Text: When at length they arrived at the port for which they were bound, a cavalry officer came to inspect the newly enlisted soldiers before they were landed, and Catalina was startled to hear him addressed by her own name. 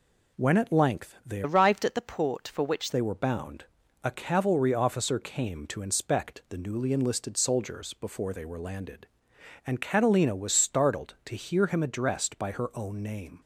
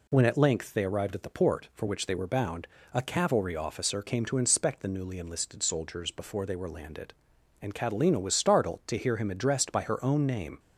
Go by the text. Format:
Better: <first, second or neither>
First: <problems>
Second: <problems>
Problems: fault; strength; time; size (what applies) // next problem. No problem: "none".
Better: second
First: changes voice from "arrived" to "which"; from 1.4 to 2.9 s; 1.5 s long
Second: none